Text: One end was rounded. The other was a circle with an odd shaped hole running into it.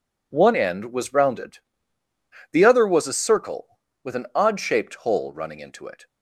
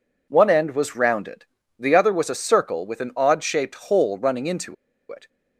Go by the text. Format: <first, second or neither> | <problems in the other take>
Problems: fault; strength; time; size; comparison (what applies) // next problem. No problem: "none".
first | pauses between "into" and "it"; at 4.7 s; 0.36 s long